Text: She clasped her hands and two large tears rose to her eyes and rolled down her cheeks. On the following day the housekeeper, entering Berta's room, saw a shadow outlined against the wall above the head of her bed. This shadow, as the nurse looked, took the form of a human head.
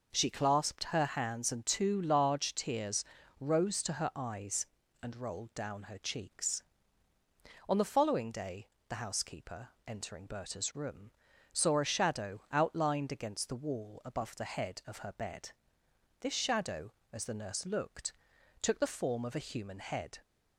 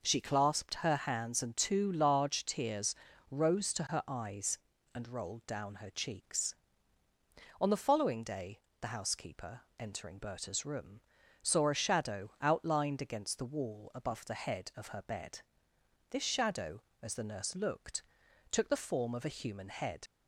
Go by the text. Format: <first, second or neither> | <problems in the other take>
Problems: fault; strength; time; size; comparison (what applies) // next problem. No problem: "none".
first | pauses between "tears" and "rose"; slight; at 2.9 s; 0.34 s long; slight in the first // pauses between "day" and "the"; slight; at 8.5 s; 0.22 s long; slight in the first // leaves "head" unfinished; at 20.0 s; 45 ms